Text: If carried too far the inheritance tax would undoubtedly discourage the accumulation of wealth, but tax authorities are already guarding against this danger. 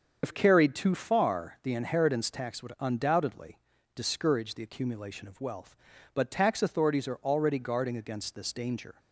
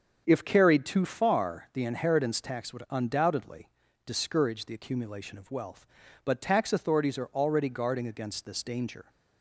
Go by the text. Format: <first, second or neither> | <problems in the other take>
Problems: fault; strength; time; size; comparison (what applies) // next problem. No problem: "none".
second | loses the start of "If"; at 0.2 s; 75 ms // starts louder than the rest; until 1.2 s; 7 dB; also in the second // pauses between "undoubtedly" and "discourage"; slight; at 3.5 s; 0.36 s long; slight in the second